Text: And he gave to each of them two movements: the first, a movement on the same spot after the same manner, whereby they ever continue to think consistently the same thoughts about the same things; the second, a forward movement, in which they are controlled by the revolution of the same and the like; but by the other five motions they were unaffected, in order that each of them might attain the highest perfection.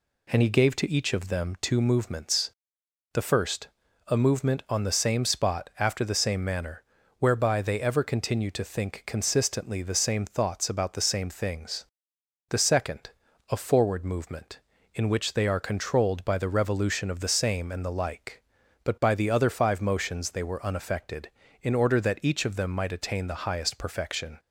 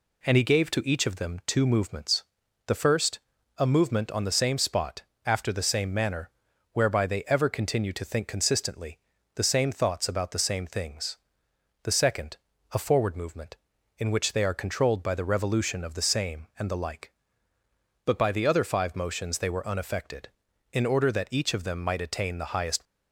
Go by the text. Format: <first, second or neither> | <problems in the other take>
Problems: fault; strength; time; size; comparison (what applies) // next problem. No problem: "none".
first | pauses between "spot" and "after"; slight; at 5.0 s; 0.22 s long // pauses between "consistently" and "the"; at 8.9 s; 0.38 s long // stops before "perfection"; at 22.8 s